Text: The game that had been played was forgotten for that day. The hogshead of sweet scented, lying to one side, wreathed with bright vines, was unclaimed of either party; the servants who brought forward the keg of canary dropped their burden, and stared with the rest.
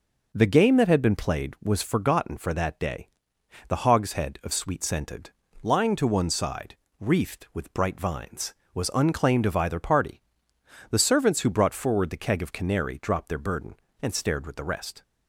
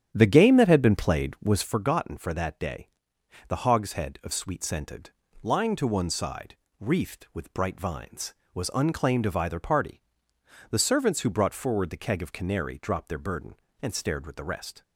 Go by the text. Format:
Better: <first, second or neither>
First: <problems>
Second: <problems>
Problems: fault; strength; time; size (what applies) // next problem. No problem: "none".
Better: first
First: none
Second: starts louder than the rest; strong; until 1.8 s; 10 dB